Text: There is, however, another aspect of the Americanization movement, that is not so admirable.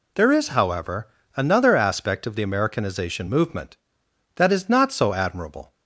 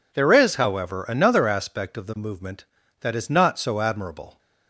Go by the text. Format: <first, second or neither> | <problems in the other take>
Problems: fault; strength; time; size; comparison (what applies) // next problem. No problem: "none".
first | skips "Americanization"; at 2.1 s